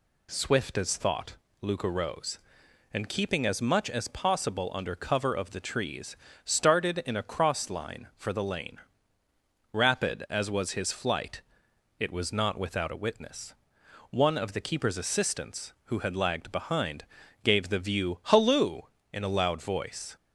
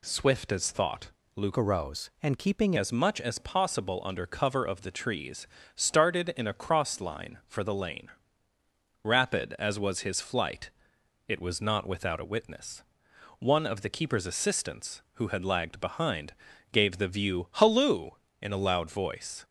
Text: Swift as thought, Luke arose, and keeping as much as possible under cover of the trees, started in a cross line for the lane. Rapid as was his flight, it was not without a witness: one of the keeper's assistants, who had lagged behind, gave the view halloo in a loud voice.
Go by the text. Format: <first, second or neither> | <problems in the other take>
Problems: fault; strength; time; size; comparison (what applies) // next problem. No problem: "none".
first | changes voice from "arose" to "keeping"; from 1.5 to 2.7 s; 1.2 s long